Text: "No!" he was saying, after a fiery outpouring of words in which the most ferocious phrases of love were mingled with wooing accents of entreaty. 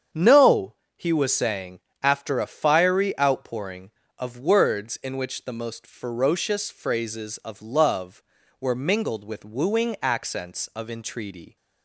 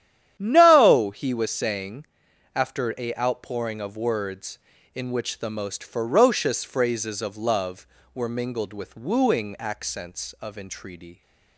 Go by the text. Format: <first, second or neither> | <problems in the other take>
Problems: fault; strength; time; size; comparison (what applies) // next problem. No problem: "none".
first | starts louder than the rest; strong; until 1.3 s; 10.5 dB; strong in the first // skips "fiery"; at 3.1 s